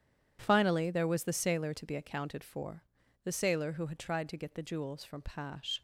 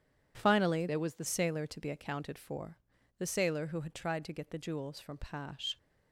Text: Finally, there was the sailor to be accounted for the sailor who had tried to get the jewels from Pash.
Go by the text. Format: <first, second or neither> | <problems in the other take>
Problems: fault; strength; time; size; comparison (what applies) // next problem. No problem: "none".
first | changes voice from "there" to "the"; from 0.8 to 1.2 s; 0.4 s long // pauses between "for" and "the"; at 2.7 s; 0.44 s long; also in the first